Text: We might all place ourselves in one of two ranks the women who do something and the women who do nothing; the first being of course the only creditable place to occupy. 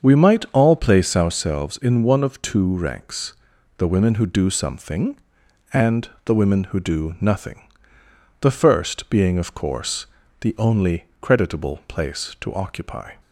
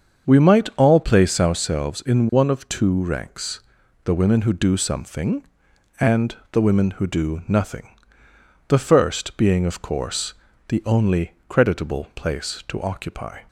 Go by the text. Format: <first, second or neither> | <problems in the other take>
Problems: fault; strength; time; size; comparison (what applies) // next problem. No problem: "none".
neither | starts louder than the rest; the same in both // pauses between "ranks" and "the"; noticeable; the same in both // pauses between "and" and "the"; slight; the same in both // pauses between "course" and "the"; the same in both // pauses between "only" and "creditable"; slight; the same in both